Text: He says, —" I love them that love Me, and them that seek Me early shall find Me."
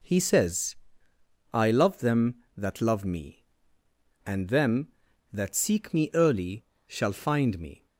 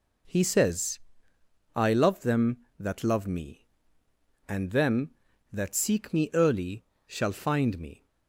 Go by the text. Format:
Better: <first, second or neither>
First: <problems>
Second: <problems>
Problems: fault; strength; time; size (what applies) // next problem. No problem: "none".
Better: neither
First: pauses between "early" and "shall"; slight; at 6.6 s; 0.24 s long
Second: pauses between "early" and "shall"; slight; at 6.8 s; 0.24 s long